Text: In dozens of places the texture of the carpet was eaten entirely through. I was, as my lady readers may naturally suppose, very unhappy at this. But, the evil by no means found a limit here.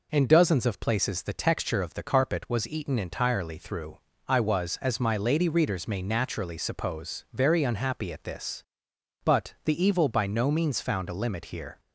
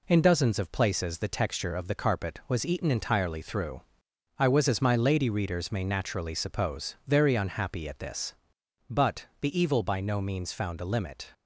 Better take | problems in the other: first | stops before "here"; at 11.3 s

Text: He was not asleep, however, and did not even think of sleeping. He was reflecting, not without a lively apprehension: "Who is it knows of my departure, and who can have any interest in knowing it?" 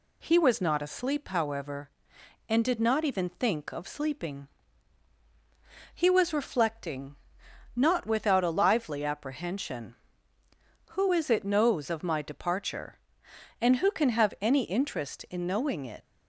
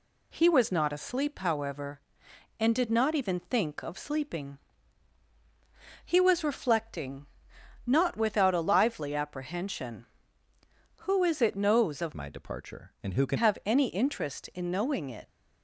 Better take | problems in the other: first | changes voice from "my" to "can"; from 12.1 to 13.3 s; 1.2 s long

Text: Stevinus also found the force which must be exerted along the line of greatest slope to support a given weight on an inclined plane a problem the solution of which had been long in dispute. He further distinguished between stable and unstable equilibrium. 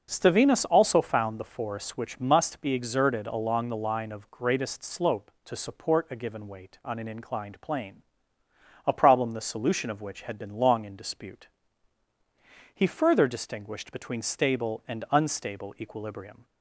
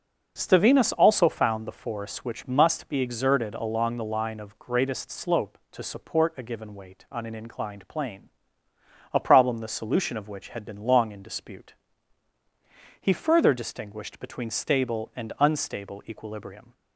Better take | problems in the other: neither | pauses between "plane" and "a"; noticeable; the same in both

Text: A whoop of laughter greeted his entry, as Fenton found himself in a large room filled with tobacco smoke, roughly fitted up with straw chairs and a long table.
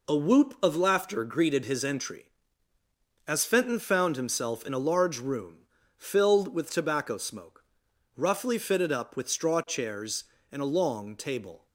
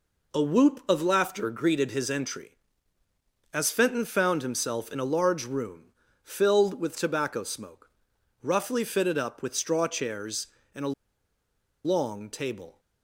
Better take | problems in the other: first | pauses between "room" and "filled"; slight; at 5.9 s; 0.32 s long; slight in the first // pauses between "a" and "long"; noticeable; at 10.9 s; 0.91 s long

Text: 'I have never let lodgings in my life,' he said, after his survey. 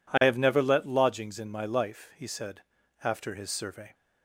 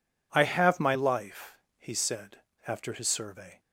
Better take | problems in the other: first | skips "never let lodgings in"; at 0.7 s

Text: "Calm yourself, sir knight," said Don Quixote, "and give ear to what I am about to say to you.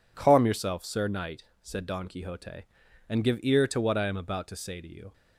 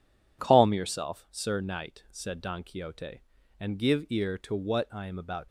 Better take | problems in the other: first | stops before "to say to you"; at 5.4 s

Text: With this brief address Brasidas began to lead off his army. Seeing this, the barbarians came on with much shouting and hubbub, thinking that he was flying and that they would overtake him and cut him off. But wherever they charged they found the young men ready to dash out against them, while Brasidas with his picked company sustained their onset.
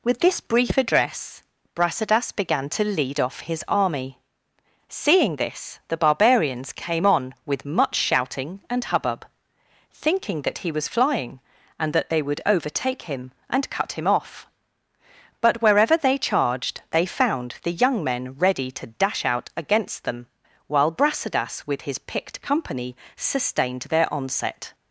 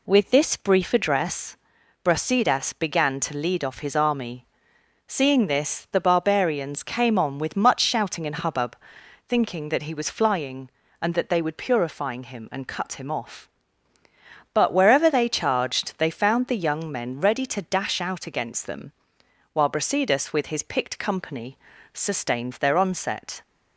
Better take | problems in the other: first | pauses between "address" and "Brasidas"; noticeable; at 1.5 s; 0.48 s long; slight in the first // says "purifying" for "overtake"; at 11.5 s // pauses between "company" and "sustained"; slight; at 21.5 s; 0.36 s long; slight in the first

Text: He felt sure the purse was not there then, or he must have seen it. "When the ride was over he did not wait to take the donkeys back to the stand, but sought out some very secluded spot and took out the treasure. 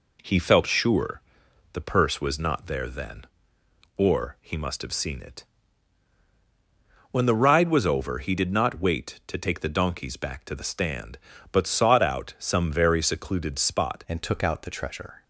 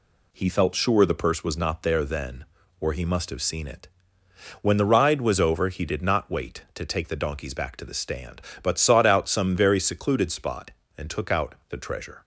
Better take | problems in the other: second | pauses between "sure" and "the"; noticeable; at 1.2 s; 0.52 s long // changes voice at "and"; from 14.0 s on; 1.2 s long

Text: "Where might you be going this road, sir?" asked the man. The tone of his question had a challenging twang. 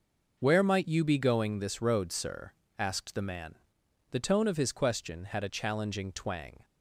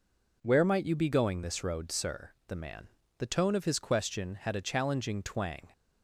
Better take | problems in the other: first | skips "asked"; at 2.3 s

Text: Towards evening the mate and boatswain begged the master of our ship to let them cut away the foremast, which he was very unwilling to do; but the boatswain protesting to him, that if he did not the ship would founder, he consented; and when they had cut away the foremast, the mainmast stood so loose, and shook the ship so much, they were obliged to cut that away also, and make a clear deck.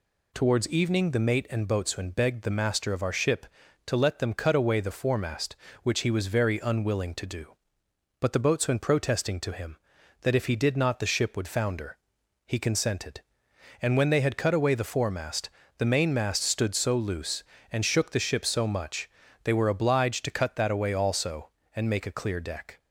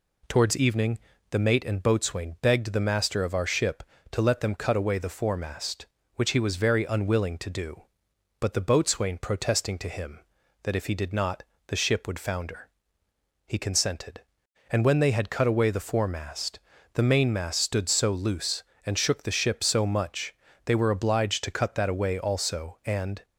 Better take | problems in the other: first | pauses between "evening" and "the"; slight; at 0.9 s; 0.32 s long // pauses between "not" and "the"; slight; at 11.4 s; 0.24 s long // stops before "make a clear deck"; at 23.2 s

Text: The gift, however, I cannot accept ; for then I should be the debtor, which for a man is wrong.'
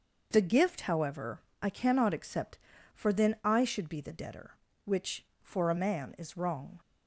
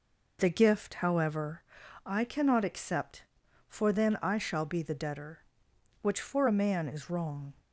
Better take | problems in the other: first | says "shall" for "should"; at 4.3 s

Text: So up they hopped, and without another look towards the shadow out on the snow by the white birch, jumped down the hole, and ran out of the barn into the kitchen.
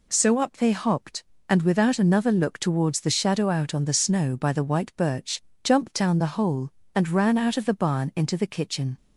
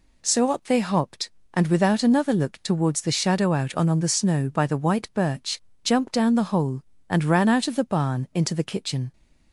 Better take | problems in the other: first | says "on" twice; at 3.8 s

